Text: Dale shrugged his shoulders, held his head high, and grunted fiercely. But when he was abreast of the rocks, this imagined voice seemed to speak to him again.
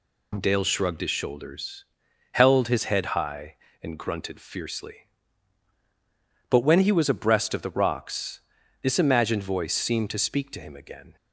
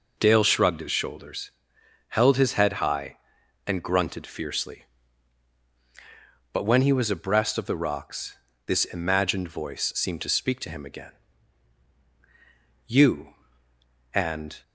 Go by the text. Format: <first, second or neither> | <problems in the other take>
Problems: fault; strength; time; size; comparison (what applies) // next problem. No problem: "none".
first | goes on to say "You and"; strong; from 12.8 s on; 1.7 s long